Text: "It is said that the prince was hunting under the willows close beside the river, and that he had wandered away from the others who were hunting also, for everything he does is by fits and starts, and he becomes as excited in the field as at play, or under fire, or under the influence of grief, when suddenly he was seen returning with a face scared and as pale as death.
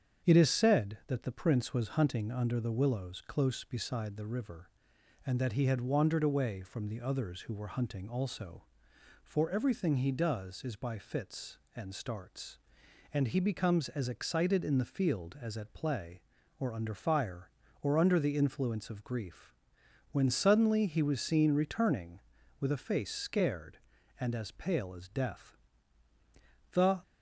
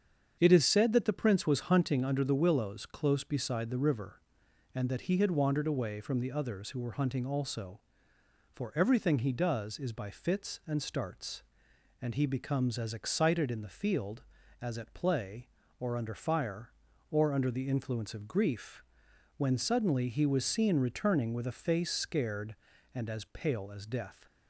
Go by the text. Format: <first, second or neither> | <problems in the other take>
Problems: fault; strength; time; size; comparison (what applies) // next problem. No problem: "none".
second | starts louder than the rest; strong; until 1.3 s; 8 dB; strong in the second // goes on to say "The"; slight; from 26.7 s on; 0.28 s long